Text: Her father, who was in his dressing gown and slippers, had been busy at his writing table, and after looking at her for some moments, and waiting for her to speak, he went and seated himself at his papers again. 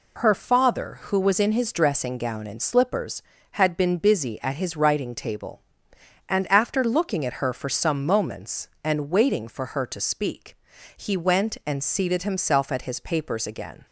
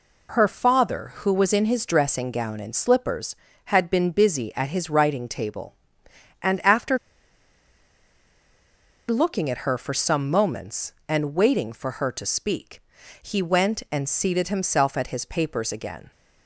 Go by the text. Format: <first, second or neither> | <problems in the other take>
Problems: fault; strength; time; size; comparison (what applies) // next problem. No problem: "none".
first | pauses between "after" and "looking"; strong; at 6.9 s; 2.1 s long